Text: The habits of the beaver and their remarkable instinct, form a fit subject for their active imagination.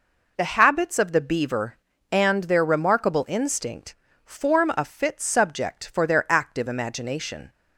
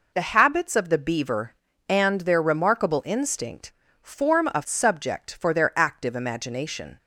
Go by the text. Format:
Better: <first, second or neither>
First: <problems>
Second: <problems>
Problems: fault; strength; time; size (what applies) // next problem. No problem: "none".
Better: first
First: none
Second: skips "fit"; at 4.6 s